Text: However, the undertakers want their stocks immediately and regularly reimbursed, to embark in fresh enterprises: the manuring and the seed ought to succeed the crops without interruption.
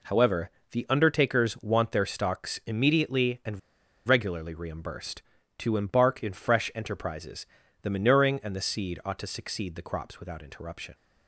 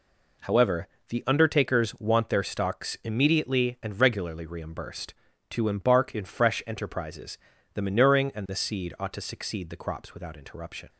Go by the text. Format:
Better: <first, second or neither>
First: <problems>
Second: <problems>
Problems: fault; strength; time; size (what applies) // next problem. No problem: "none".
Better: second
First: pauses between "and" and "regularly"; noticeable; at 3.5 s; 0.48 s long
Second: none